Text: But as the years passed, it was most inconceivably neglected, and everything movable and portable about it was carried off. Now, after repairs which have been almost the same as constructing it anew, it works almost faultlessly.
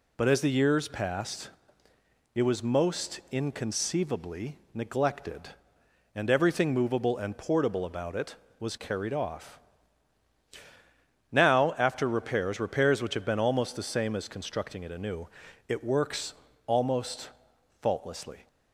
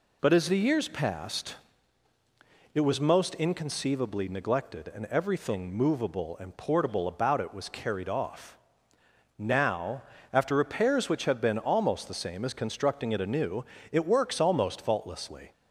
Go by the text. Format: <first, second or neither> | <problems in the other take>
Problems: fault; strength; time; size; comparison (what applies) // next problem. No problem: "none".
second | pauses between "inconceivably" and "neglected"; slight; at 4.5 s; 0.16 s long // says "repairs" twice; at 12.5 s // pauses between "works" and "almost"; slight; at 16.3 s; 0.32 s long // pauses between "almost" and "faultlessly"; noticeable; at 17.2 s; 0.52 s long